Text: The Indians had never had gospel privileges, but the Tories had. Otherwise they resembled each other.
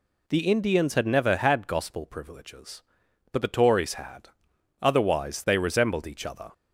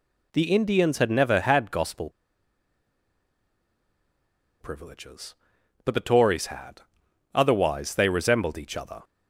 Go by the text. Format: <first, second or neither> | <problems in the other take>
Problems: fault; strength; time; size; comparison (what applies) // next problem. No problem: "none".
first | pauses between "gospel" and "privileges"; strong; at 2.1 s; 2.5 s long